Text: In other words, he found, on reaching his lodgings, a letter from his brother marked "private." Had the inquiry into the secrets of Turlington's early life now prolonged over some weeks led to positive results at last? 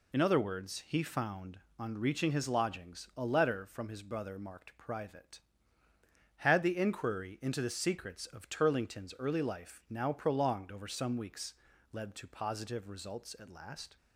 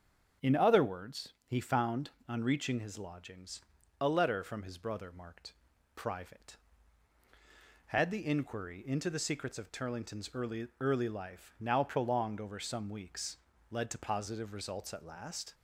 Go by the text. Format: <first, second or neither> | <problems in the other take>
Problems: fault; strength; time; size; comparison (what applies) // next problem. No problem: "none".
first | starts louder than the rest; until 1.6 s; 7 dB // pauses between "marked" and "private"; at 5.5 s; 0.44 s long // says "early" twice; at 10.7 s // pauses between "weeks" and "led"; slight; at 13.3 s; 0.34 s long; also in the first